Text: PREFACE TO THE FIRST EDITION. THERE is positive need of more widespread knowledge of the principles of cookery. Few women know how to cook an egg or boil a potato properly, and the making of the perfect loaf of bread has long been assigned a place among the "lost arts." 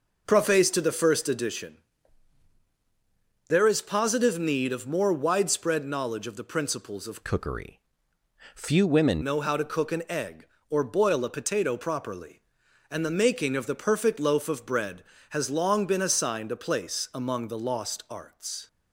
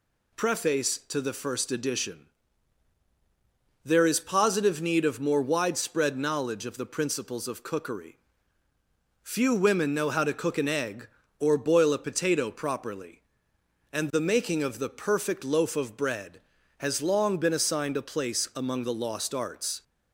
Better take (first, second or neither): second